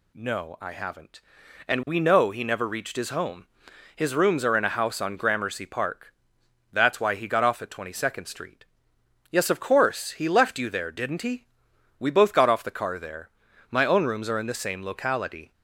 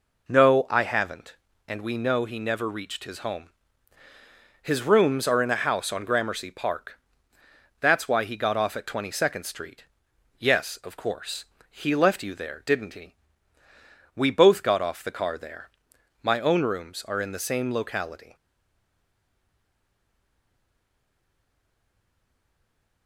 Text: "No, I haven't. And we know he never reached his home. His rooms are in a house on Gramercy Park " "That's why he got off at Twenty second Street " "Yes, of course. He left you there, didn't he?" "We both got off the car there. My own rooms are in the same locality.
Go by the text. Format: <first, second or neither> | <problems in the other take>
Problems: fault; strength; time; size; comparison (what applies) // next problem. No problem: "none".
first | stays silent after the last word; strong; from 18.3 s on; 4.7 s long